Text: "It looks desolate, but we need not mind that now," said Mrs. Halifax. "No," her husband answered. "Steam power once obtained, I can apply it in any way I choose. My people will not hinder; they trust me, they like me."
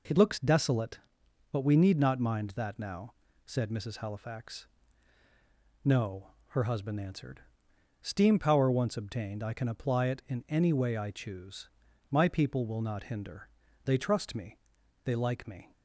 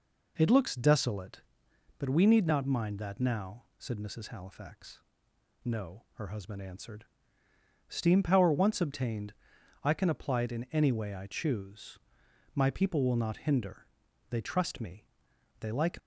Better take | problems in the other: first | stops before "me"; at 15.9 s

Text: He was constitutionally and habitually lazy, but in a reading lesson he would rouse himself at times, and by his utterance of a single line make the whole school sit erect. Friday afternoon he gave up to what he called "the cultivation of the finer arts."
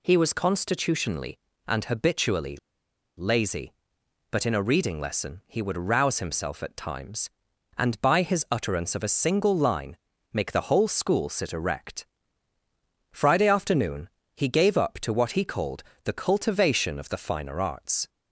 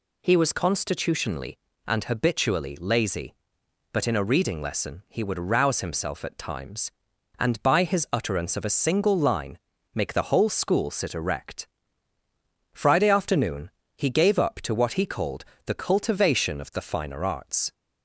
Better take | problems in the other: second | pauses between "habitually" and "lazy"; noticeable; at 2.5 s; 0.62 s long // pauses between "line" and "make"; slight; at 9.9 s; 0.36 s long; slight in the second // pauses between "afternoon" and "he"; slight; at 14.0 s; 0.26 s long; slight in the second // pauses between "called" and "the"; slight; at 15.8 s; 0.22 s long; slight in the second

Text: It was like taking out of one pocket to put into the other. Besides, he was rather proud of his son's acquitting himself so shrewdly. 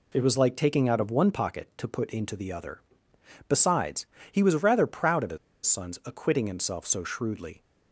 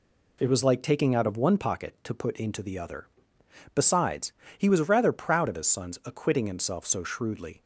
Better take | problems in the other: second | pauses between "his" and "son's"; slight; at 5.3 s; 0.28 s long

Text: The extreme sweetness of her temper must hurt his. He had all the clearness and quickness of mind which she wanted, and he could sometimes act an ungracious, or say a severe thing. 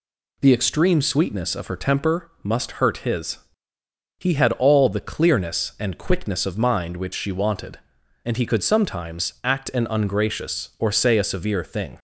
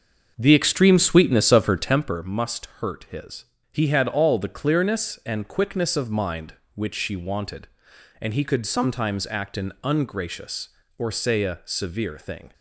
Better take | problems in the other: first | starts louder than the rest; until 2.3 s; 6.5 dB

